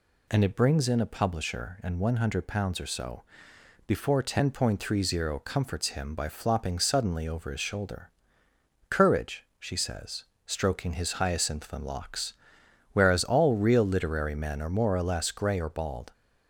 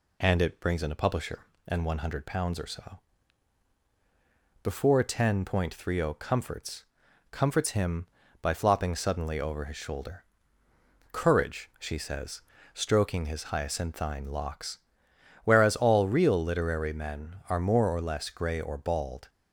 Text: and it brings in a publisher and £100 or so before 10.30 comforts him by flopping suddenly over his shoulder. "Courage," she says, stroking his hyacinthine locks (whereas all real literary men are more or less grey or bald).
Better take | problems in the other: first | pauses between "so" and "before"; strong; at 2.9 s; 1.6 s long; noticeable in the first // says "comforts" twice; at 7.2 s

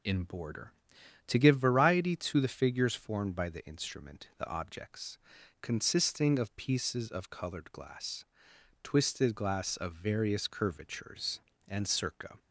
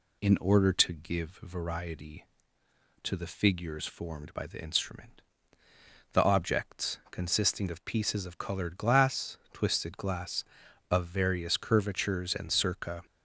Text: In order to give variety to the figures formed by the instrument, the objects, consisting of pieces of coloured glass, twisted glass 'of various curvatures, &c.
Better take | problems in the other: second | says "border" for "order"; at 0.2 s

